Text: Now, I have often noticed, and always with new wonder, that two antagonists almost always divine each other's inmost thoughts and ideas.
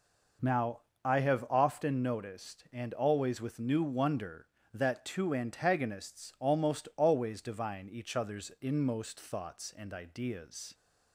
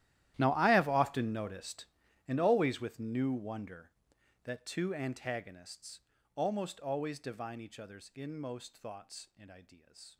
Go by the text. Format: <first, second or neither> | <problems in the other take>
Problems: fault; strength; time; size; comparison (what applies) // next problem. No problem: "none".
first | gets quieter; strong; throughout; 20.5 dB // pauses between "antagonists" and "almost"; slight; at 6.0 s; 0.34 s long